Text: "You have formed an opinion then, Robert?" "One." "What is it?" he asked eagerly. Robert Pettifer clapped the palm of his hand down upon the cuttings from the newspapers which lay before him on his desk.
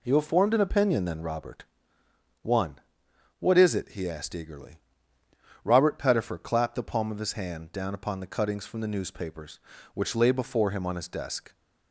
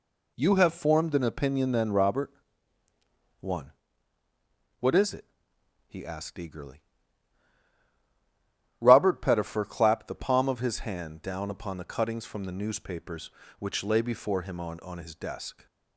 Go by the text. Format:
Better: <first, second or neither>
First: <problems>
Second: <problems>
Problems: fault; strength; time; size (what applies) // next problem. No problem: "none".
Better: first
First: none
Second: says "on" twice; at 14.7 s